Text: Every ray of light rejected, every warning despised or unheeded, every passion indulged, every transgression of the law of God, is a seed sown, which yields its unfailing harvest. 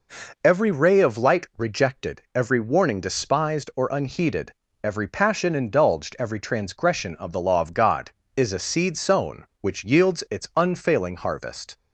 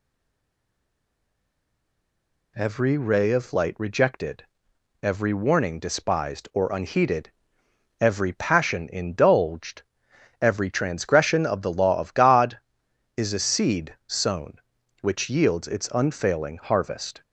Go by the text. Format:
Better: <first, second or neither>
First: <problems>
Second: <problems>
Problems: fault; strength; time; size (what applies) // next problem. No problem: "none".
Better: first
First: none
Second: stays silent before the first word; strong; until 2.5 s; 2.5 s long